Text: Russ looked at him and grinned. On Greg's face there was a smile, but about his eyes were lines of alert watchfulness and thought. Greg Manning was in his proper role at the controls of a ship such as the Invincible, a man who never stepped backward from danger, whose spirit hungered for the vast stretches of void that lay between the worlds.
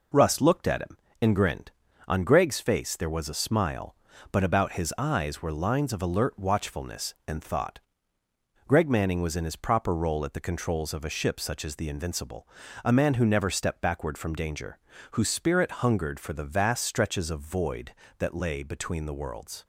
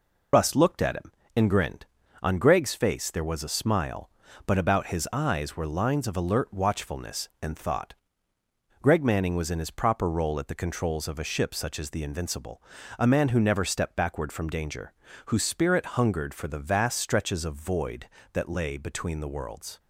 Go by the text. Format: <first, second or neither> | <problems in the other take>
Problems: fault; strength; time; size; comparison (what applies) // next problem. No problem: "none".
first | loses the start of "Russ"; at 0.3 s; 60 ms